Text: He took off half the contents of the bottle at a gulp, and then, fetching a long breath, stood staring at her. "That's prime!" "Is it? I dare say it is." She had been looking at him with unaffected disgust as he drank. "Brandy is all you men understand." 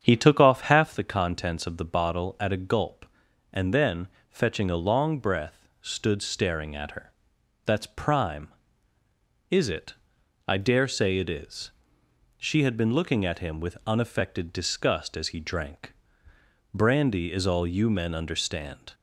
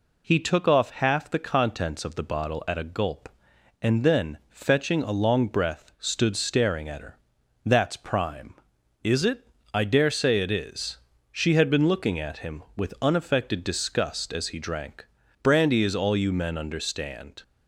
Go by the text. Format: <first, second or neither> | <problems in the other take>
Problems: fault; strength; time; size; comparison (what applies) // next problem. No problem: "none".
second | starts louder than the rest; strong; until 1.1 s; 8 dB